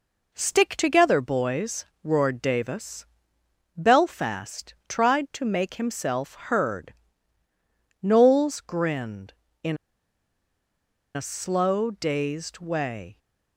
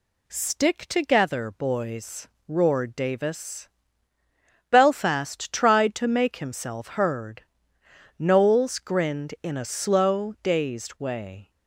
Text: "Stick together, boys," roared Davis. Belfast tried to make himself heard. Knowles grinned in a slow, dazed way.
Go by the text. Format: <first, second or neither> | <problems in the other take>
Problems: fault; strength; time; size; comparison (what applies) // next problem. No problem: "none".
second | pauses between "Belfast" and "tried"; slight; at 4.7 s; 0.16 s long // pauses between "in" and "a"; strong; at 9.7 s; 1.3 s long